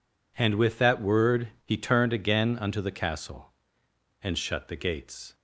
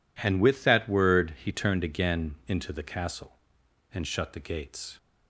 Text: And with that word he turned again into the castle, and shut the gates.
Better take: second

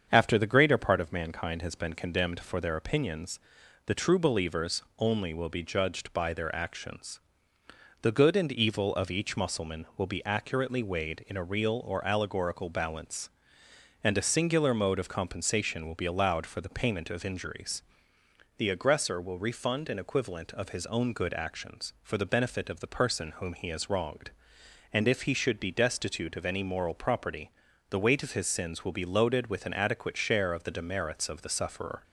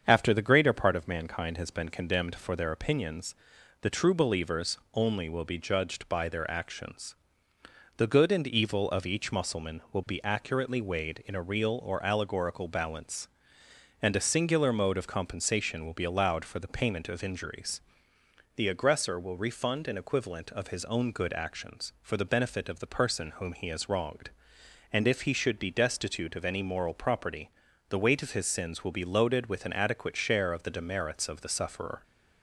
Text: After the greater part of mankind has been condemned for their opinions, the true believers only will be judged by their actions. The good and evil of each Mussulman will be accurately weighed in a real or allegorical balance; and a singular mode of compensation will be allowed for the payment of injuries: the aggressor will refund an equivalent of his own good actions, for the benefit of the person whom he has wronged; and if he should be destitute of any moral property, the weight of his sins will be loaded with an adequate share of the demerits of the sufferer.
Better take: neither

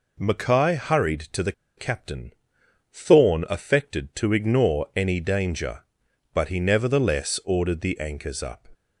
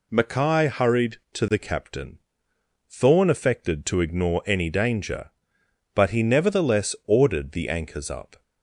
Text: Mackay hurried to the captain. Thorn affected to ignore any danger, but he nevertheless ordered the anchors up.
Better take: second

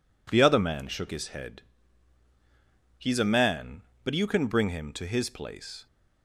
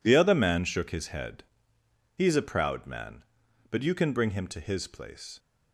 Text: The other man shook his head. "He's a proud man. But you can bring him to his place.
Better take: second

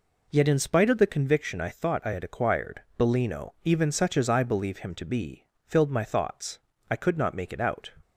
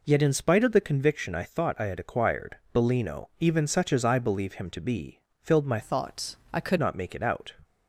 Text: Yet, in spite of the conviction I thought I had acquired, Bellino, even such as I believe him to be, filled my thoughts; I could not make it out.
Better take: first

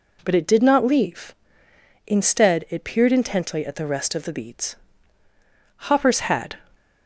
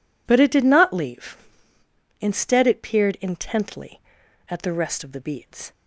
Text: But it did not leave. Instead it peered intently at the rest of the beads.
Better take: second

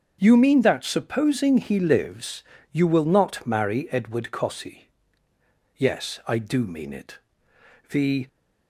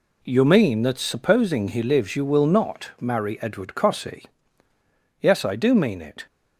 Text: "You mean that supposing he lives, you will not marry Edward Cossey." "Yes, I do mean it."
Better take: second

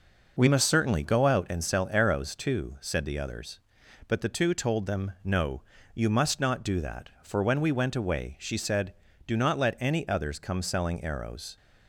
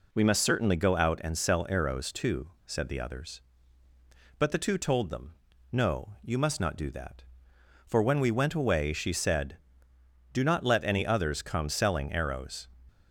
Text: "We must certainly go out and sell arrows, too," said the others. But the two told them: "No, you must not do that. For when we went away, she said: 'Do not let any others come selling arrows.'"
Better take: neither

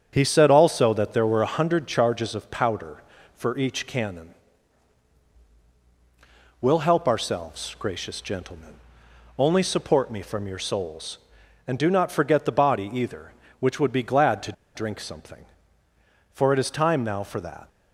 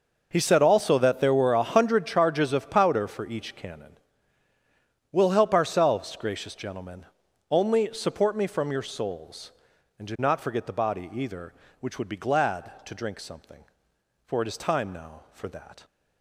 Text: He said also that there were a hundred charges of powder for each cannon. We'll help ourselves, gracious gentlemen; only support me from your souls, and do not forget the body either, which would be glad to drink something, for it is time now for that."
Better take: second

